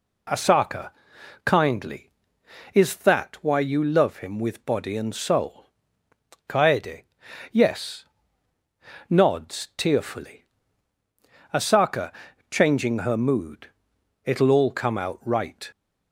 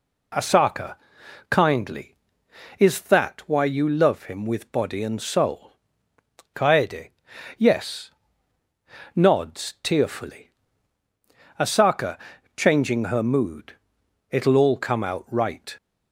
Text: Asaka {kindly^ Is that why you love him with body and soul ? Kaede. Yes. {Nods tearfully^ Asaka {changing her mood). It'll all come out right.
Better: neither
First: pauses between "tearfully" and "Asaka"; at 10.4 s; 1.0 s long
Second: pauses between "tearfully" and "Asaka"; at 10.5 s; 1.0 s long

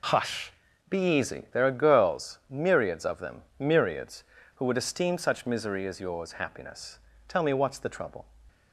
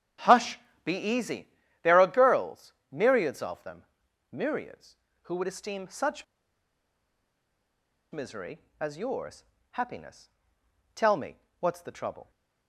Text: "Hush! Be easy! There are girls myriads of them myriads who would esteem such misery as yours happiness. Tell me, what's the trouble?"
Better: first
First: pauses between "them" and "myriads"; slight; at 3.4 s; 0.18 s long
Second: starts louder than the rest; strong; until 1.4 s; 8.5 dB // pauses between "girls" and "myriads"; slight; at 2.7 s; 0.18 s long // pauses between "them" and "myriads"; noticeable; at 3.8 s; 0.48 s long // pauses between "such" and "misery"; strong; at 6.2 s; 1.8 s long // pauses between "yours" and "happiness"; slight; at 9.4 s; 0.28 s long

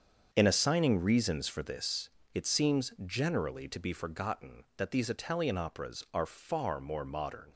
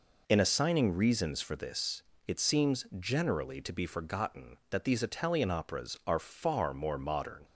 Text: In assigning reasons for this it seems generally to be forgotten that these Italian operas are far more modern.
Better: second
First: gets quieter; strong; throughout; 10.5 dB // pauses between "this" and "it"; slight; at 2.0 s; 0.26 s long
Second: pauses between "this" and "it"; slight; at 2.0 s; 0.26 s long

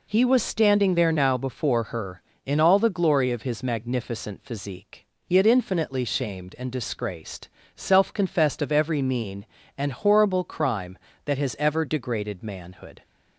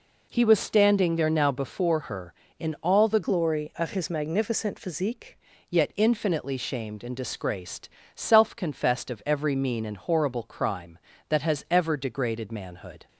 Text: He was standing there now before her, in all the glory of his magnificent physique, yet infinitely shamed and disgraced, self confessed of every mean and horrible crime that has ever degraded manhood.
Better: first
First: none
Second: changes voice from "glory" to "physique"; from 3.2 to 5.3 s; 2.1 s long

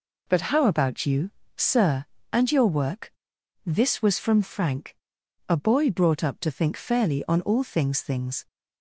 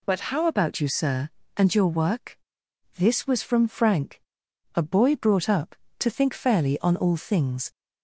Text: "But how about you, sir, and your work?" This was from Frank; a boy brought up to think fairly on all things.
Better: second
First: says "things" twice; at 8.0 s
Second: none

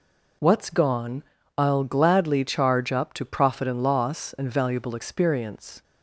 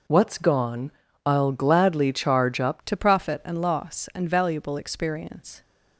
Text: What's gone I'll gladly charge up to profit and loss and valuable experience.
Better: first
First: pauses between "gone" and "I'll"; slight; at 1.2 s; 0.34 s long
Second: pauses between "gone" and "I'll"; slight; at 0.9 s; 0.34 s long // changes voice at "to"; from 2.8 s on; 2.8 s long

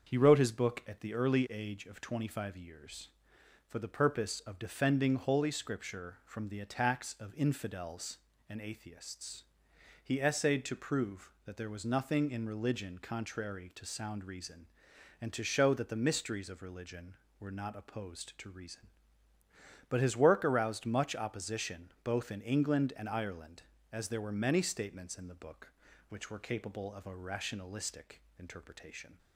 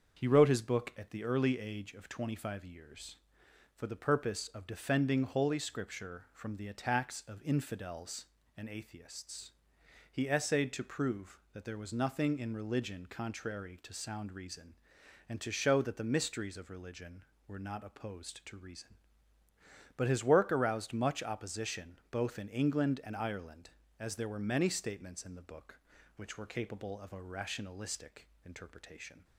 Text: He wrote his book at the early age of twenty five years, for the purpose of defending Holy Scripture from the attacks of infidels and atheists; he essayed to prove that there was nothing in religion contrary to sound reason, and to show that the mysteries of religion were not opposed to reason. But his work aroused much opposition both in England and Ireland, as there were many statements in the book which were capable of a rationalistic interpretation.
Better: neither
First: starts louder than the rest; until 1.1 s; 6.5 dB // pauses between "rationalistic" and "interpretation"; slight; at 28.2 s; 0.18 s long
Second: starts louder than the rest; until 1.2 s; 6.5 dB // pauses between "rationalistic" and "interpretation"; slight; at 28.2 s; 0.18 s long

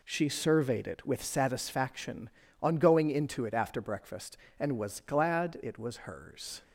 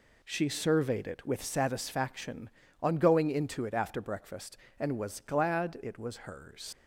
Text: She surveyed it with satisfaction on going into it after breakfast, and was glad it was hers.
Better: first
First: none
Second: leaves "hers" unfinished; at 6.7 s; 95 ms

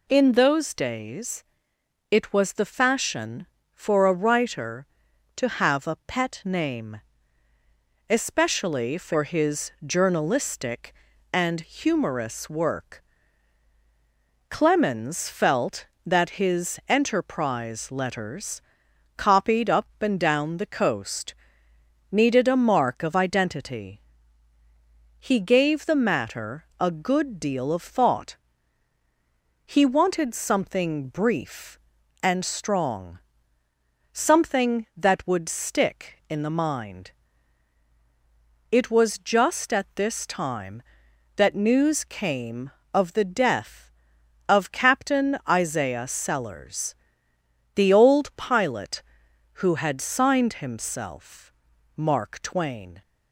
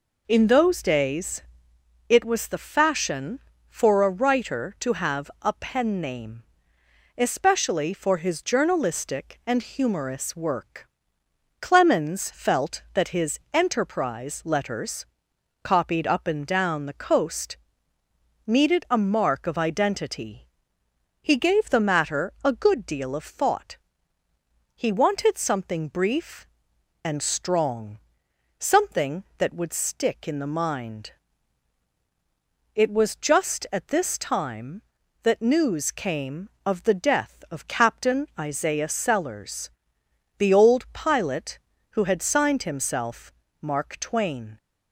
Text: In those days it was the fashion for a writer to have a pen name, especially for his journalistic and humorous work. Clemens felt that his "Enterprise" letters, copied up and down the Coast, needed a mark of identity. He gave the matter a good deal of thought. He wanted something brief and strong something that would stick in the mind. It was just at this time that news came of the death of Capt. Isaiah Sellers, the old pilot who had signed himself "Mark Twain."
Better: second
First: pauses between "days" and "it"; noticeable; at 1.4 s; 0.68 s long // says "pet" for "pen"; at 6.0 s // pauses between "strong" and "something"; at 33.1 s; 1.0 s long // pauses between "himself" and "Mark"; noticeable; at 51.5 s; 0.46 s long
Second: pauses between "days" and "it"; noticeable; at 1.4 s; 0.66 s long // pauses between "strong" and "something"; noticeable; at 27.9 s; 0.58 s long // pauses between "himself" and "Mark"; slight; at 43.3 s; 0.30 s long

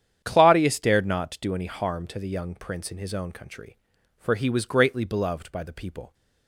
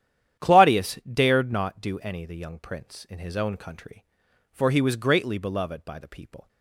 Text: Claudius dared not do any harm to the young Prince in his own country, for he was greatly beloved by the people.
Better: first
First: starts louder than the rest; strong; until 1.2 s; 9 dB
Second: starts louder than the rest; strong; until 1.5 s; 10.5 dB // skips "harm to"; at 2.2 s

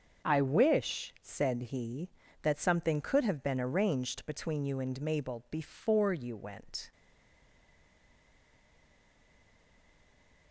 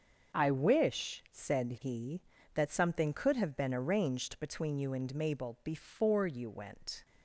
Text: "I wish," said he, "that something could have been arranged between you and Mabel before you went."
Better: second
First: starts louder than the rest; until 1.3 s; 6.5 dB // stays silent after the last word; strong; from 6.9 s on; 3.6 s long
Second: starts louder than the rest; until 1.4 s; 6.5 dB

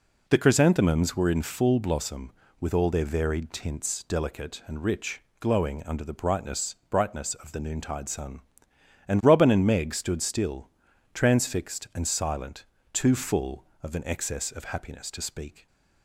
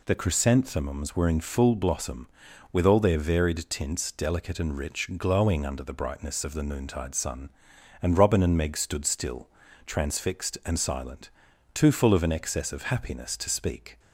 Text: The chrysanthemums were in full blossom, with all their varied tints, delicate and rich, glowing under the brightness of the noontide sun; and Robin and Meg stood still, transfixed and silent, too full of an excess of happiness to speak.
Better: second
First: says "brightness" twice; at 6.9 s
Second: none

